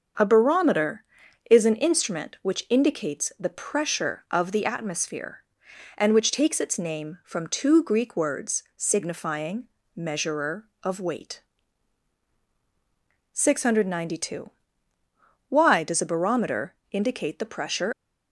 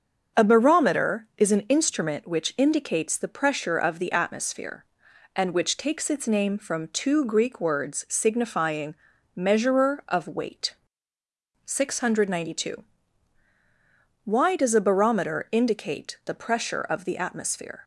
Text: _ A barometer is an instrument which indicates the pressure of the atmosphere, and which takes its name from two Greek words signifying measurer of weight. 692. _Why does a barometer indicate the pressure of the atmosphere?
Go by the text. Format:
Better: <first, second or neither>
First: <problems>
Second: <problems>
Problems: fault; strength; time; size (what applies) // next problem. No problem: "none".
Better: second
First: starts louder than the rest; until 1.6 s; 6.5 dB // pauses between "signifying" and "measurer"; slight; at 9.6 s; 0.30 s long // pauses between "barometer" and "indicate"; slight; at 16.7 s; 0.18 s long // stops before "of the atmosphere"; at 17.9 s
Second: starts louder than the rest; until 1.4 s; 7 dB // pauses between "signifying" and "measurer"; at 8.9 s; 0.40 s long